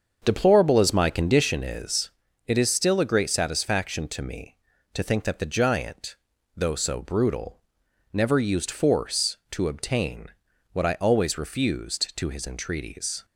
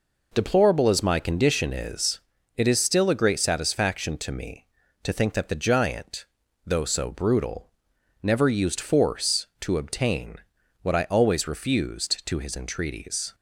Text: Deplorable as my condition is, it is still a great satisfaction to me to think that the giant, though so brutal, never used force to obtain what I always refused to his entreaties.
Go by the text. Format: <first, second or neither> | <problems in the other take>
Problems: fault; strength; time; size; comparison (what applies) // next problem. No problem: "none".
second | starts louder than the rest; until 1.5 s; 7 dB // pauses between "obtain" and "what"; at 10.2 s; 0.44 s long; also in the second